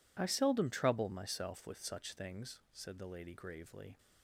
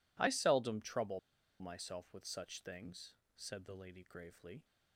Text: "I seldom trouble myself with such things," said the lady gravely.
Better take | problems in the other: first | pauses between "trouble" and "myself"; at 1.1 s; 0.40 s long

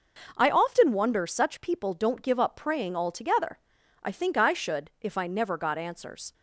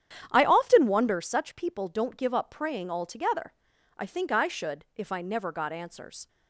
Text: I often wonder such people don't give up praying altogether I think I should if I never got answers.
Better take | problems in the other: first | starts louder than the rest; strong; until 1.3 s; 10 dB // pauses between "altogether" and "I"; at 3.5 s; 0.44 s long; also in the first

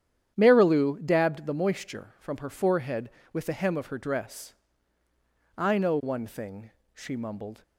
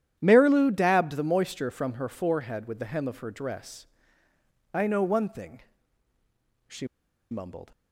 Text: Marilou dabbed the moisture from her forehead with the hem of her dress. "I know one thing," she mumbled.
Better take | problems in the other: first | starts louder than the rest; strong; until 1.2 s; 10.5 dB; strong in the first // pauses between "she" and "mumbled"; at 6.8 s; 0.43 s long

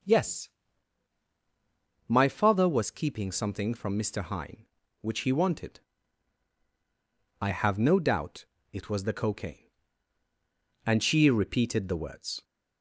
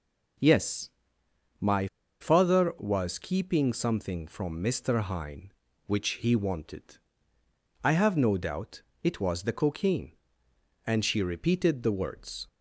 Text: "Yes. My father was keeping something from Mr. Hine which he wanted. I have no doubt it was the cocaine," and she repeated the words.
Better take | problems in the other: first | pauses between "My" and "father"; slight; at 1.8 s; 0.32 s long // pauses between "doubt" and "it"; slight; at 8.8 s; 0.20 s long; slight in the first

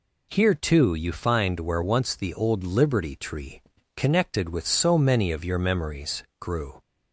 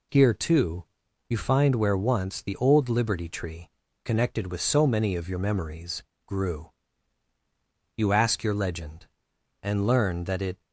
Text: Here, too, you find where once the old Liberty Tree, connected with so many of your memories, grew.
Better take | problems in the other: first | goes on to say "You ask your legend and learn that it"; strong; from 7.9 s on; 2.6 s long

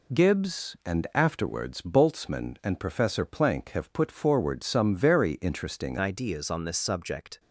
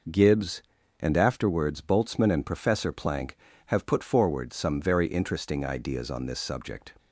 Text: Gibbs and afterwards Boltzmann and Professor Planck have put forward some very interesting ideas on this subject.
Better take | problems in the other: second | changes voice at "ideas"; from 5.9 s on; 1.4 s long

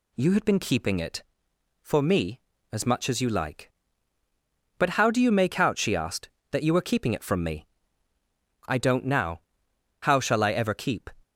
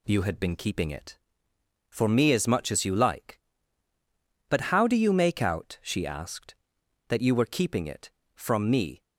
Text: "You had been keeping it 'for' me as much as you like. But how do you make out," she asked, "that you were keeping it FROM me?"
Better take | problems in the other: second | goes on to say "I don't now How shall I ever keep"; strong; from 8.6 s on; 2.4 s long

